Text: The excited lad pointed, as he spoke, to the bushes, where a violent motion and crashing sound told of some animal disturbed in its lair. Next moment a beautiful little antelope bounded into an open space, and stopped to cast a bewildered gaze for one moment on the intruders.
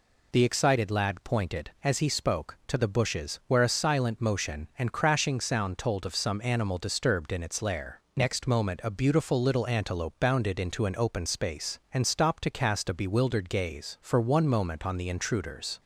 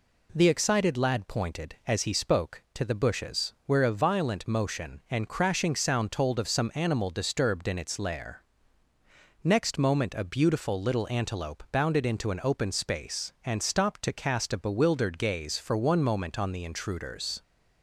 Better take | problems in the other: second | says "silent" for "violent"; at 3.6 s

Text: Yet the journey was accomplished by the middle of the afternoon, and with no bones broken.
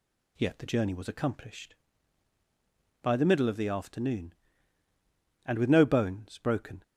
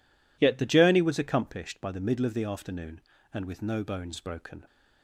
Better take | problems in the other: neither | none

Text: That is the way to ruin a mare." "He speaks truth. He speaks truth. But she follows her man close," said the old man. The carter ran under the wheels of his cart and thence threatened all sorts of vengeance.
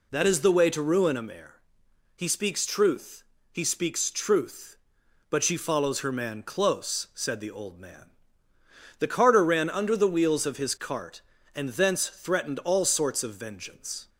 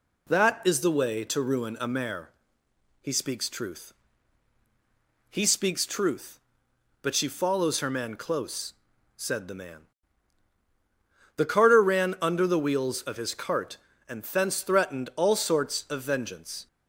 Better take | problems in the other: first | skips "old"; at 9.5 s

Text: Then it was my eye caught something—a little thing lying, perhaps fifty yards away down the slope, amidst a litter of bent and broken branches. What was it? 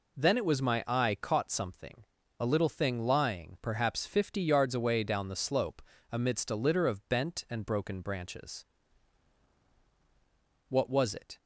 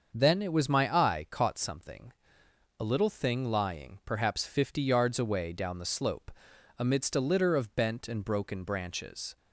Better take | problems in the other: first | starts louder than the rest; until 1.1 s; 6.5 dB // stops before "What was it"; at 9.3 s

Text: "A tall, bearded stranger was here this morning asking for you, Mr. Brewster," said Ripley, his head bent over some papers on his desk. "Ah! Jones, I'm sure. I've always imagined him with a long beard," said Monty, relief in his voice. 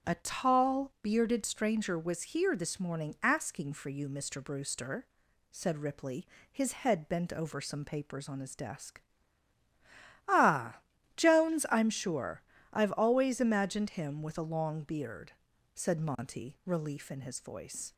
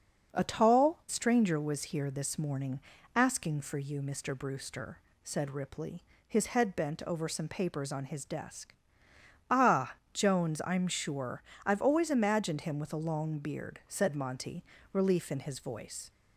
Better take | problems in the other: first | starts louder than the rest; until 1.3 s; 6.5 dB; strong in the first // skips "bearded"; at 1.0 s // pauses between "morning" and "asking"; at 2.7 s; 0.38 s long

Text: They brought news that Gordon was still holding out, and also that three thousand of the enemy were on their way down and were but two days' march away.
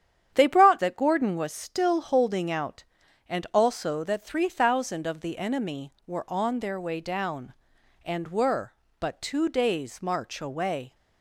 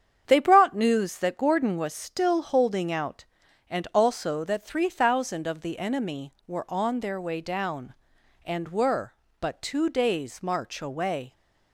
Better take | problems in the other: second | starts louder than the rest; strong; until 1.3 s; 9 dB; strong in the second // skips "news"; at 0.7 s

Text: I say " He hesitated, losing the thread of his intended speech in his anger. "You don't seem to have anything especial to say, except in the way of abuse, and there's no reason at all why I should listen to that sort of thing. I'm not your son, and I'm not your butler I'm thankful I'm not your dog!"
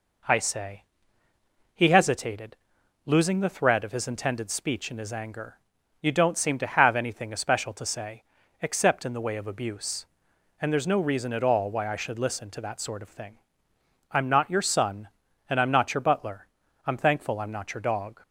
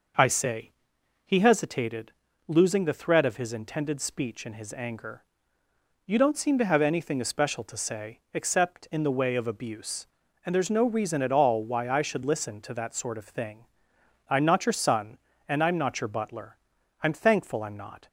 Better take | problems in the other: first | pauses between "butler" and "I'm"; at 16.5 s; 0.44 s long; also in the first // stops before "your dog"; at 18.0 s

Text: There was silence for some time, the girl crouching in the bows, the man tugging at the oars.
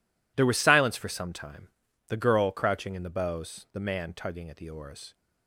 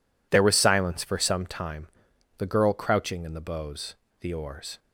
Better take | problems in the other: first | skips "man tugging at the"; at 4.3 s

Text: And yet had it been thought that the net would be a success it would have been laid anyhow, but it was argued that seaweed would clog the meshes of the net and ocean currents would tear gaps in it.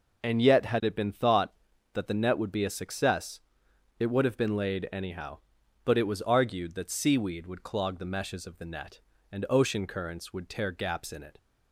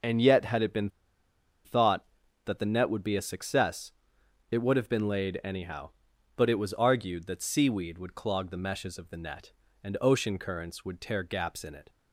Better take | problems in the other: first | pauses between "been" and "thought"; noticeable; at 0.8 s; 0.75 s long // pauses between "success" and "it"; noticeable; at 3.9 s; 0.60 s long; noticeable in the first

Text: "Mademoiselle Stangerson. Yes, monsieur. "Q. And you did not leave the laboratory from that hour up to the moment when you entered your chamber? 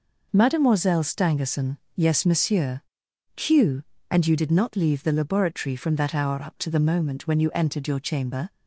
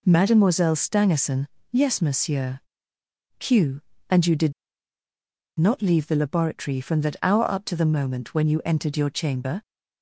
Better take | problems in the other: first | pauses between "did" and "not"; at 4.5 s; 1.0 s long

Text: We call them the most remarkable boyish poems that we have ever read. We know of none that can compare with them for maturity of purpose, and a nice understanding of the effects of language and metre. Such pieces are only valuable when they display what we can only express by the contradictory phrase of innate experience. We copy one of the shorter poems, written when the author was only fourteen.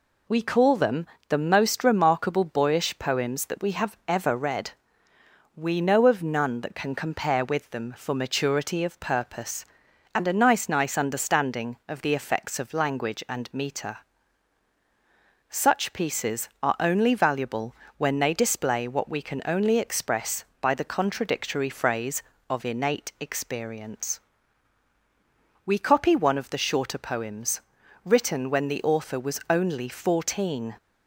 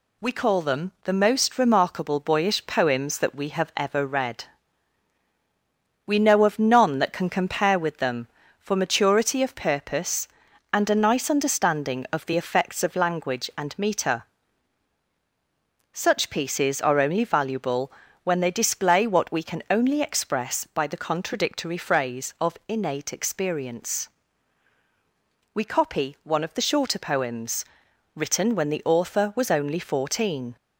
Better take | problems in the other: second | pauses between "them" and "the"; slight; at 1.0 s; 0.22 s long // says "nice" twice; at 10.6 s // pauses between "valuable" and "when"; slight; at 17.7 s; 0.24 s long; slight in the second

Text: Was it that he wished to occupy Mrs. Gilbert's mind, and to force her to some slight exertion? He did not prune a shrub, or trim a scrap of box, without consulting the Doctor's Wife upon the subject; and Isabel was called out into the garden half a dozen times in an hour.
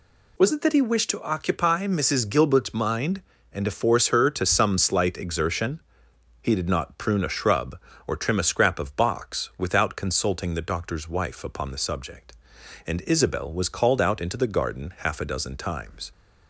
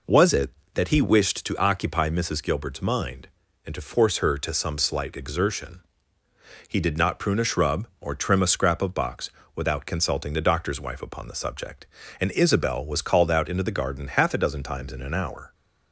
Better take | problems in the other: second | stops before "in an hour"; at 16.1 s

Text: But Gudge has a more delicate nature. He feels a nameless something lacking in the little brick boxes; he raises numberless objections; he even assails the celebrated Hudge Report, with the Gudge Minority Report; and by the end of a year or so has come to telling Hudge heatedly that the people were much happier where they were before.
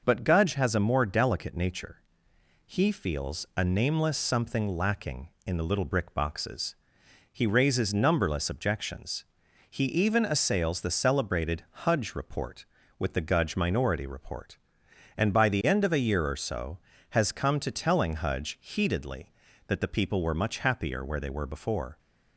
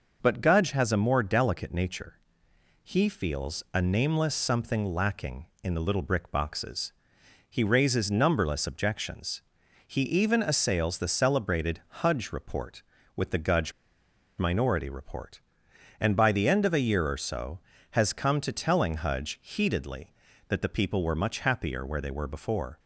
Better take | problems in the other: first | pauses between "celebrated" and "Hudge"; slight; at 11.8 s; 0.24 s long; slight in the first // pauses between "Gudge" and "Minority"; noticeable; at 13.7 s; 0.66 s long

